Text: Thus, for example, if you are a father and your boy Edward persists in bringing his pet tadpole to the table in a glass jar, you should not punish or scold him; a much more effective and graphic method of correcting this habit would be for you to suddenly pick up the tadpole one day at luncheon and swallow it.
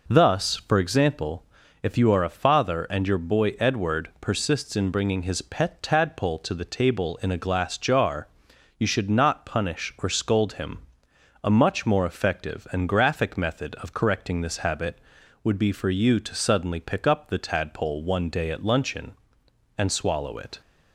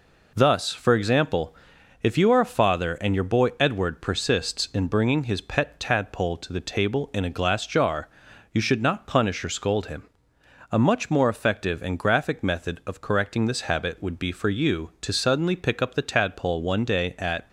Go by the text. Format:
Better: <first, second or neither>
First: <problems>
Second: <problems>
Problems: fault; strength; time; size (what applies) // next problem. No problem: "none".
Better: first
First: none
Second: stops before "luncheon and swallow it"; at 17.4 s